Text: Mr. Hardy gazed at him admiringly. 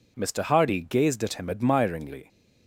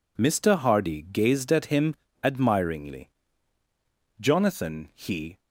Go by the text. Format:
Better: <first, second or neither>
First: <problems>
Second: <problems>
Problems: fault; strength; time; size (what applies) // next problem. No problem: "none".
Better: first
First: none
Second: pauses between "him" and "admiringly"; slight; at 1.9 s; 0.30 s long // goes on to say "Jonathan he"; noticeable; from 4.1 s on; 1.2 s long